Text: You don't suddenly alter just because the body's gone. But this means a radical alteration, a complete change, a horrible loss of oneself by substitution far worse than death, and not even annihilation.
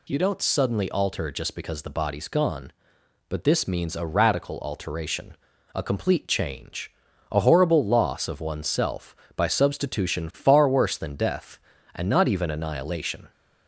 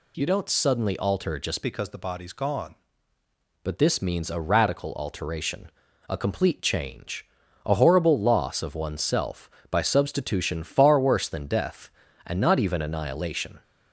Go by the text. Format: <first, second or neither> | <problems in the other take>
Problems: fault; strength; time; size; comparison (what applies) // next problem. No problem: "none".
first | changes voice from "because" to "gone"; from 1.6 to 2.7 s; 1.1 s long